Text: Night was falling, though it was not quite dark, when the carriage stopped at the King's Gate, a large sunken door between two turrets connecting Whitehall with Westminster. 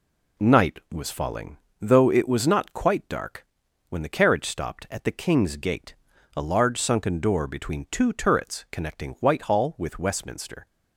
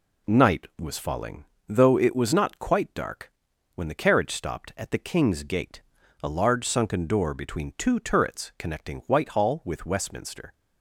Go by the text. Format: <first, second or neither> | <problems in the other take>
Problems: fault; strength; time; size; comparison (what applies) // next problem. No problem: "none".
neither | none